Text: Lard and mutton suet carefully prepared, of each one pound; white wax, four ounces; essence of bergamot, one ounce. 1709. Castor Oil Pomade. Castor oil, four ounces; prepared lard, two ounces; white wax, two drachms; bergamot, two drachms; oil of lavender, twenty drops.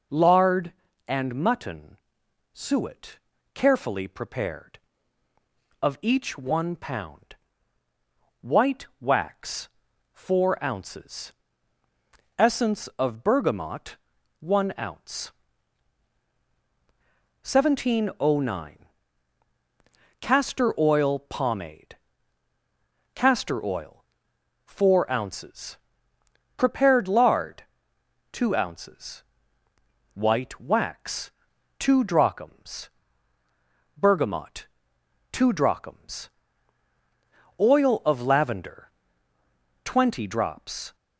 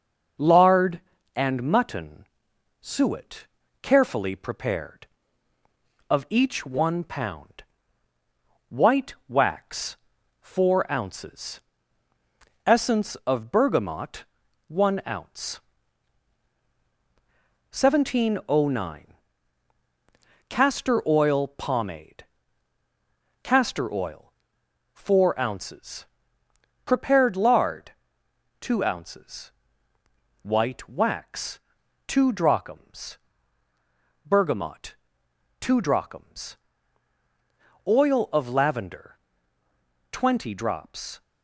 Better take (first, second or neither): first